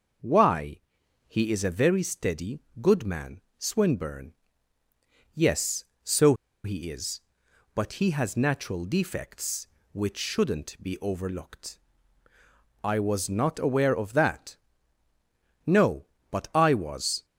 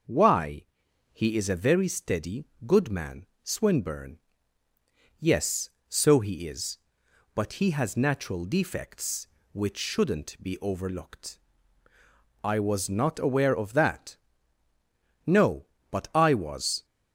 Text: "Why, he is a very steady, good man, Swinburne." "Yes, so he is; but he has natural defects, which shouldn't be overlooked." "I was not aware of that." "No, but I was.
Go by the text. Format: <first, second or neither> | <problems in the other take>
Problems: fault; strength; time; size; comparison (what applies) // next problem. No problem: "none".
second | pauses between "so" and "he"; slight; at 6.3 s; 0.29 s long